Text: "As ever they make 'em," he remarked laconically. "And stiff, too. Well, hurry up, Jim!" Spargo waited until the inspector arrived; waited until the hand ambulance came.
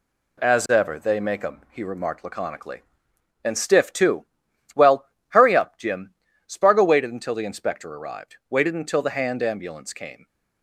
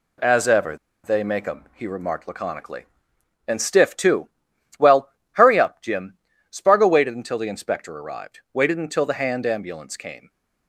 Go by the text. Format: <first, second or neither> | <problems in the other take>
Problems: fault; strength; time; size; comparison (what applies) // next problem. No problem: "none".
first | pauses between "ever" and "they"; slight; at 0.7 s; 0.28 s long